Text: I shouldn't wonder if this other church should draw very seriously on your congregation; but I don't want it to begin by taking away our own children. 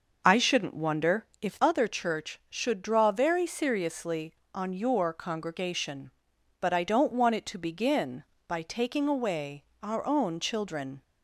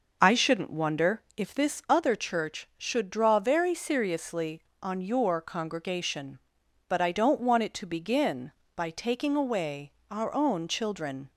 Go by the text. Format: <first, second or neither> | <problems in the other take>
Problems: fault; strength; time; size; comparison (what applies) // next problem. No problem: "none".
second | skips "this"; at 1.5 s // pauses between "away" and "our"; slight; at 9.6 s; 0.22 s long; slight in the second